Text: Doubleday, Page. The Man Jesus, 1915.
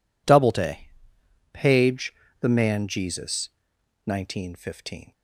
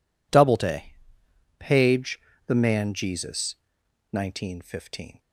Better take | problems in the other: neither | none

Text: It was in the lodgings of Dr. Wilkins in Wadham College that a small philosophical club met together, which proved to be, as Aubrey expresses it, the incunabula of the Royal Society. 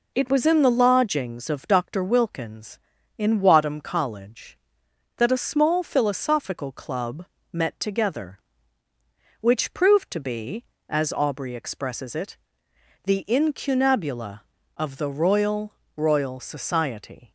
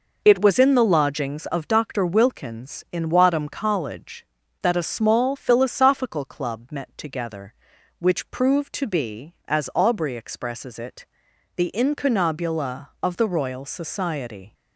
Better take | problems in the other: second | pauses between "club" and "met"; slight; at 7.2 s; 0.26 s long // says "Royal" twice; at 15.9 s

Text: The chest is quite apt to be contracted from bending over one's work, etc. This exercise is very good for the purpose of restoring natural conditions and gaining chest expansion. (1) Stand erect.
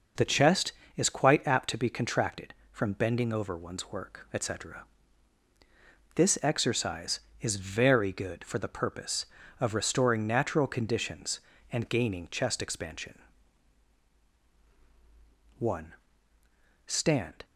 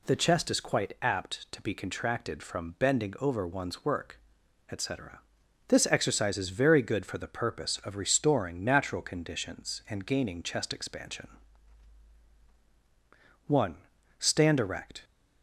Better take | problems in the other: second | stops before "erect"; at 17.4 s

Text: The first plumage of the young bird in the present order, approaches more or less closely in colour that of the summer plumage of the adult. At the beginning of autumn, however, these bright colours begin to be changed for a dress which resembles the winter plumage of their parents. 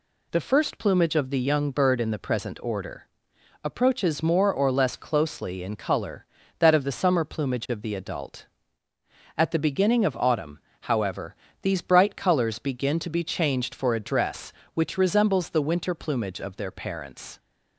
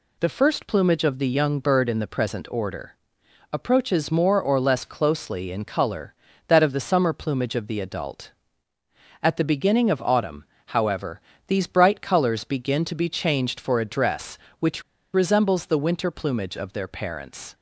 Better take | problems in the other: first | pauses between "which" and "resembles"; slight; at 14.8 s; 0.31 s long

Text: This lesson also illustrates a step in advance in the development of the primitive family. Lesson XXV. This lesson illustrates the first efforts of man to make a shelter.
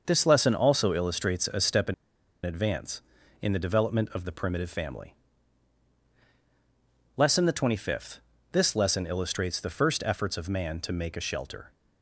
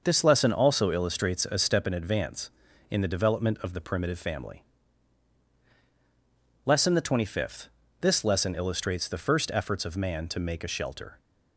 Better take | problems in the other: second | starts louder than the rest; noticeable; until 1.0 s; 6 dB; noticeable in the second // pauses between "in" and "advance"; noticeable; at 1.9 s; 0.49 s long

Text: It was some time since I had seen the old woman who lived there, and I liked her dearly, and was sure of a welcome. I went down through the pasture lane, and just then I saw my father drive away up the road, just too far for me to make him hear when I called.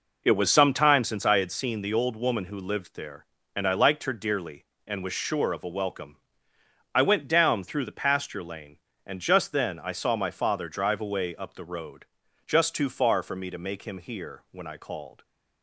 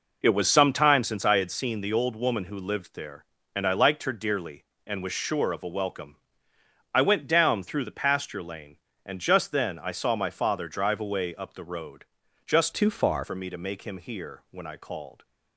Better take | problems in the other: first | changes voice from "too" to "far"; from 12.7 to 13.2 s; 0.5 s long

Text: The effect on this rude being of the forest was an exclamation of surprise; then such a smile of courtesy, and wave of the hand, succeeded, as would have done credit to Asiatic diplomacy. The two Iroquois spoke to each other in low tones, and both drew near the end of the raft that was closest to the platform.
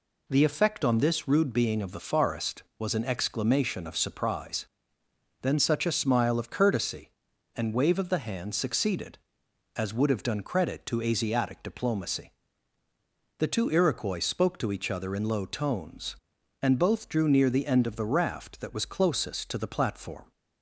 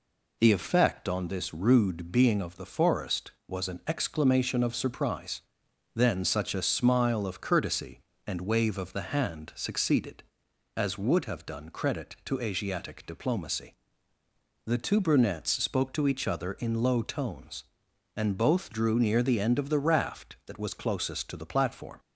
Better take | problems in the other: first | says "Brunettes" for "Iroquois"; at 15.0 s

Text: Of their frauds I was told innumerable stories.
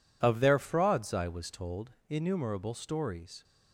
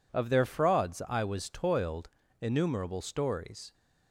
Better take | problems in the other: first | says "toiled" for "told"; at 1.5 s

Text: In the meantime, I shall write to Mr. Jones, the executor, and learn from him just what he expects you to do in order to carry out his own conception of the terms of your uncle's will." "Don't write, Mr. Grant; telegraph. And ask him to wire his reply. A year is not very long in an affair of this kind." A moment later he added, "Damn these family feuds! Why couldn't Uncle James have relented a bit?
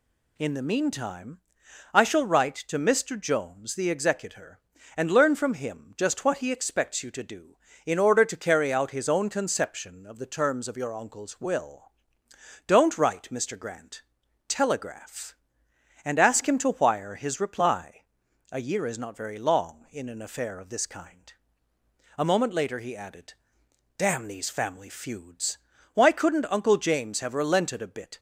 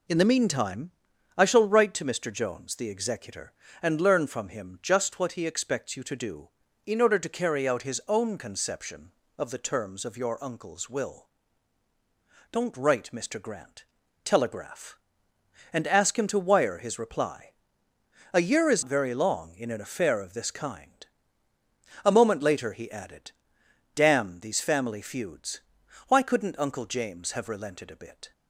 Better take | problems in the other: first | skips "not"; at 18.8 s

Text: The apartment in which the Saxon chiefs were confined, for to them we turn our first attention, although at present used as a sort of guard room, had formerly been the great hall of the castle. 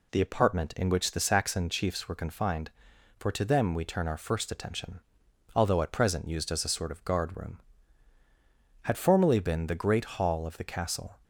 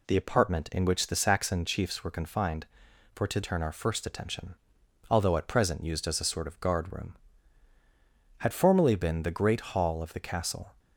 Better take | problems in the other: first | skips "them we"; at 3.4 s

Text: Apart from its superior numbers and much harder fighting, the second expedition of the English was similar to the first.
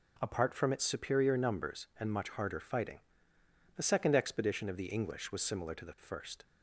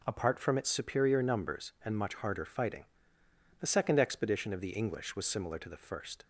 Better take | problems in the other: neither | none

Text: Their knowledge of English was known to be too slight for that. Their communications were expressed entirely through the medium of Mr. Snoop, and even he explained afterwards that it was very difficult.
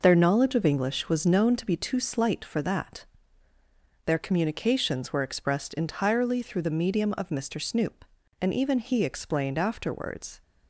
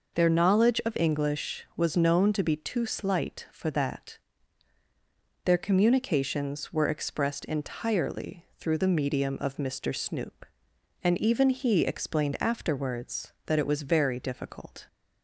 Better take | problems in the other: second | stops before "that it was very difficult"; at 10.4 s

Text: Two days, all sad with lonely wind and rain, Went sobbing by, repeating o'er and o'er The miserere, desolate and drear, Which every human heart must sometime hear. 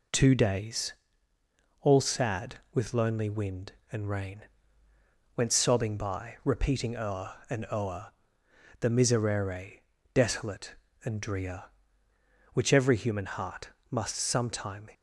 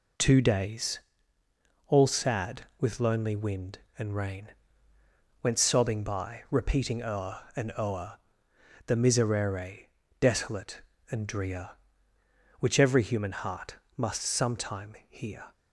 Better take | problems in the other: second | pauses between "o'er" and "The"; noticeable; at 8.1 s; 0.68 s long; noticeable in the second // pauses between "heart" and "must"; slight; at 13.6 s; 0.22 s long; slight in the second // stops before "hear"; at 14.9 s

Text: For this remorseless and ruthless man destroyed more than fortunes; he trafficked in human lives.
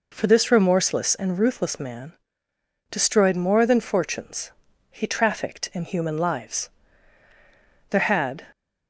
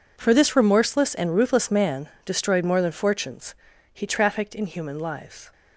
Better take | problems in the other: second | pauses between "man" and "destroyed"; noticeable; at 2.1 s; 0.78 s long; slight in the second // goes on to say "There had"; from 7.8 s on; 0.56 s long

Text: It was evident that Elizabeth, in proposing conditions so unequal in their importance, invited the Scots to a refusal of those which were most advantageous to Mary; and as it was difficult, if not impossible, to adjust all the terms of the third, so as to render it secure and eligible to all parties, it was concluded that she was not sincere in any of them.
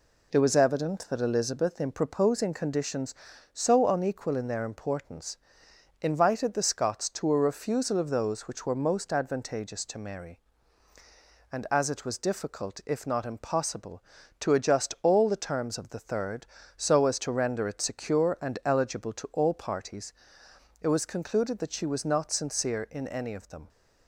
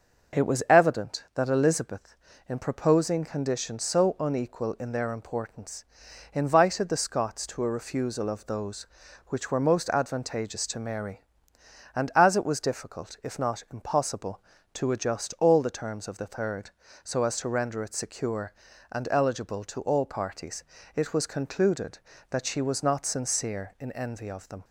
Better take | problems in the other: first | says "envy" for "any"; at 23.9 s

